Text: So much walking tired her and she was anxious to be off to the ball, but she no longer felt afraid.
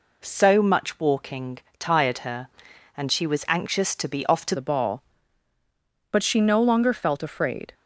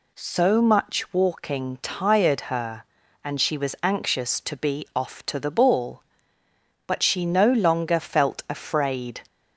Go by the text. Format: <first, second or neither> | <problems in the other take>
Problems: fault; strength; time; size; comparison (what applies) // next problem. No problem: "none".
second | pauses between "walking" and "tired"; slight; at 1.5 s; 0.22 s long // changes voice at "the"; from 4.5 s on; 3.2 s long